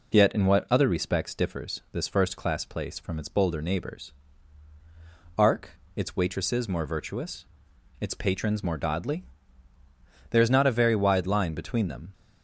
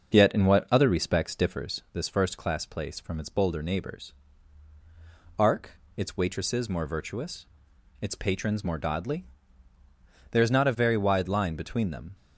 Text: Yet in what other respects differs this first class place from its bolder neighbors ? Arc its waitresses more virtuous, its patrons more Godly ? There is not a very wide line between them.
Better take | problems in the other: first | starts louder than the rest; noticeable; until 1.9 s; 6 dB // pauses between "Arc" and "its"; slight; at 5.7 s; 0.26 s long; slight in the first

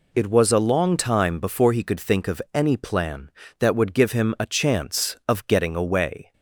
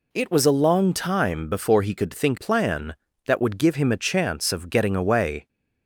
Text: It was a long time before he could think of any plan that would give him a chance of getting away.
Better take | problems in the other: first | skips "of any"; at 2.3 s

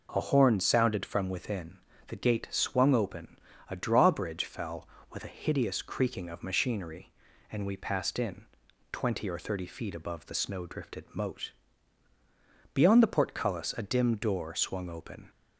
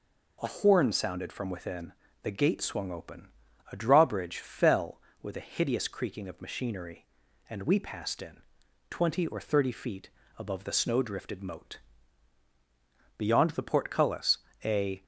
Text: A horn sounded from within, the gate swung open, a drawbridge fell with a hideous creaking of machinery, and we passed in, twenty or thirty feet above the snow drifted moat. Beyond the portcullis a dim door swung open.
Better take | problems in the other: first | pauses between "feet" and "above"; slight; at 10.0 s; 0.28 s long // pauses between "portcullis" and "a"; slight; at 14.3 s; 0.26 s long // stops before "dim door swung open"; at 15.0 s

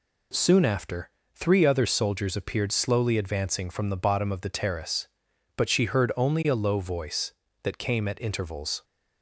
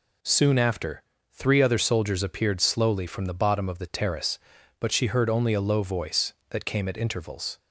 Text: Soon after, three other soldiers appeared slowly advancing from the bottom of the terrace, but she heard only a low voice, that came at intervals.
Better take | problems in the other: first | skips "advancing"; at 3.0 s

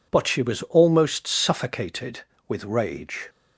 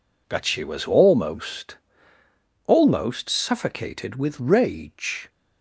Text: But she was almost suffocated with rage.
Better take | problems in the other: first | says "almost" twice; at 2.6 s

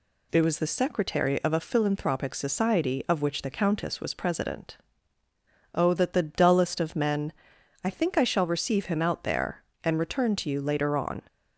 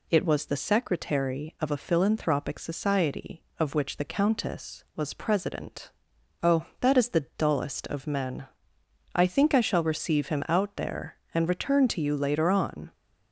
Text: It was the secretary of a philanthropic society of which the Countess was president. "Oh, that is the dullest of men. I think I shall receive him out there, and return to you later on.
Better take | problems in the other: second | skips "is"; at 6.1 s

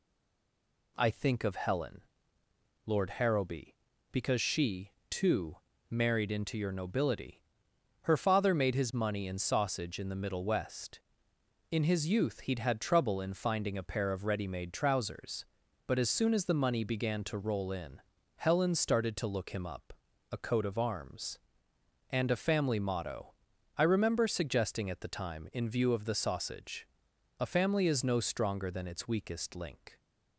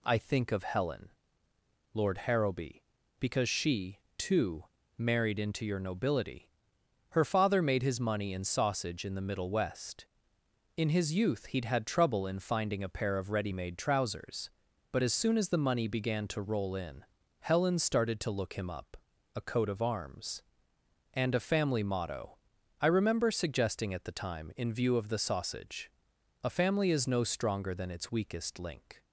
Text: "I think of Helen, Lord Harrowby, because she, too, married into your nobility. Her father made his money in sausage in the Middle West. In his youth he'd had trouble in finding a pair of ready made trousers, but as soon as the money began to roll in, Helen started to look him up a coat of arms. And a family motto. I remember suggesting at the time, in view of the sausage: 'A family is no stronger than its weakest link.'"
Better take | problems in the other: second | stays silent before the first word; slight; until 0.9 s; 0.9 s long // pauses between "up" and "a"; at 19.9 s; 0.40 s long; also in the second

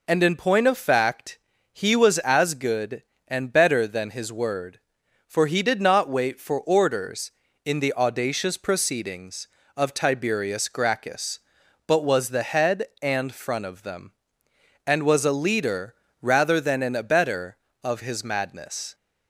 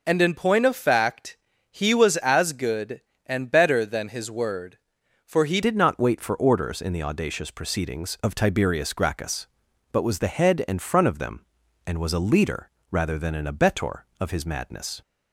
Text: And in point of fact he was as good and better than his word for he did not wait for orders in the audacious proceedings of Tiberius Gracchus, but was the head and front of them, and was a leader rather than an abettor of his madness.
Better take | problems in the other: first | pauses between "fact" and "he"; slight; at 1.3 s; 0.34 s long; slight in the first // changes voice at "did"; from 5.6 s on; 9.4 s long // pauses between "leader" and "rather"; slight; at 12.6 s; 0.22 s long; slight in the first

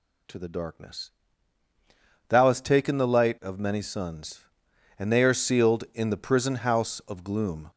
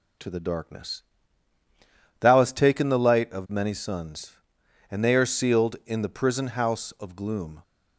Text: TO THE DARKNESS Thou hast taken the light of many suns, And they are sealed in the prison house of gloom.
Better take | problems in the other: second | gets louder; throughout; 3.5 dB // pauses between "DARKNESS" and "Thou"; at 1.0 s; 1.2 s long; also in the second

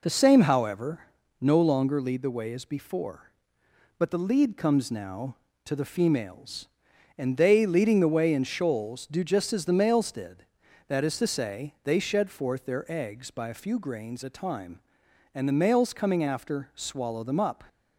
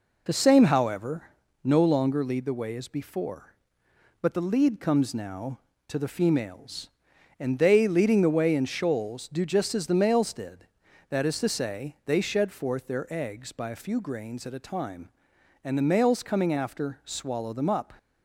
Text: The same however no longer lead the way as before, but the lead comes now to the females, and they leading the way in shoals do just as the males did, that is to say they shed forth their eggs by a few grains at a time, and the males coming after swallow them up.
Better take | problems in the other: second | pauses between "however" and "no"; slight; at 1.0 s; 0.34 s long; slight in the second // skips "at"; at 14.2 s

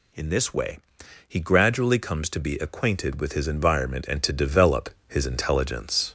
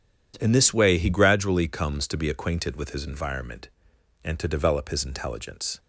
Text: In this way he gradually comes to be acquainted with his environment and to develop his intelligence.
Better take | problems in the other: second | gets louder; slight; throughout; 3 dB // pauses between "way" and "he"; noticeable; at 0.7 s; 0.48 s long // pauses between "develop" and "his"; slight; at 4.9 s; 0.18 s long

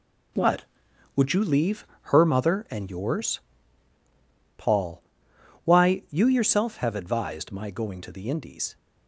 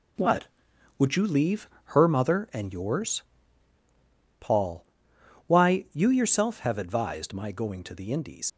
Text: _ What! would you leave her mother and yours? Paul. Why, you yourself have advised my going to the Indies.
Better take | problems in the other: first | pauses between "leave" and "her"; slight; at 1.6 s; 0.16 s long; slight in the first // leaves "Indies" unfinished; at 8.4 s; 85 ms

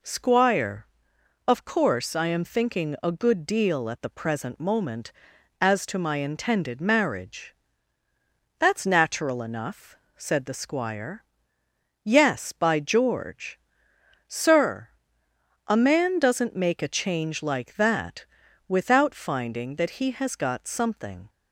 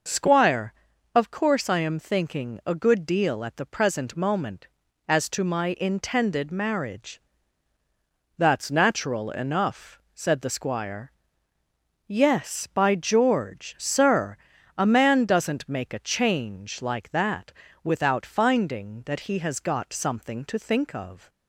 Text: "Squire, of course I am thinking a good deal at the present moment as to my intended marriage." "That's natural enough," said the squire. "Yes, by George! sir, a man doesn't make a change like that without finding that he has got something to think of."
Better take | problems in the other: second | pauses between "that" and "without"; at 18.2 s; 0.42 s long; slight in the second // stops before "to think of"; at 21.2 s

